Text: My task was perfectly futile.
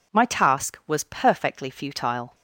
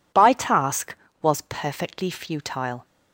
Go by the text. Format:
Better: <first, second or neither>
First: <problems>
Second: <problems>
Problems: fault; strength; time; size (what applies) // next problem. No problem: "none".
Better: first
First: none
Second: says "By" for "My"; at 0.1 s